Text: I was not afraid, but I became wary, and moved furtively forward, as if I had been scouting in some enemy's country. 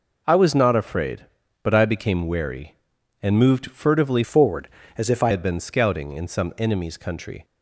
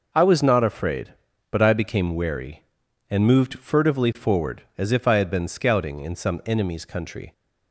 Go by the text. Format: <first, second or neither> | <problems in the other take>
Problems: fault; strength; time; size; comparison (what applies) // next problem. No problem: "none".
second | changes voice from "forward" to "I"; from 4.2 to 5.3 s; 1.1 s long